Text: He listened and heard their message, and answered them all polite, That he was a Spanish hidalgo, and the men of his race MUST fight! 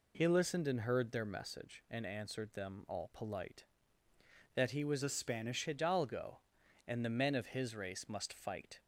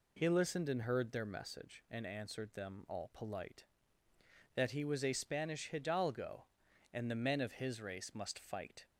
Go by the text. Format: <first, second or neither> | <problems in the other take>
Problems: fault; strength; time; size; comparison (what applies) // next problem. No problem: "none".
second | changes voice from "a" to "Spanish"; from 5.0 to 5.6 s; 0.6 s long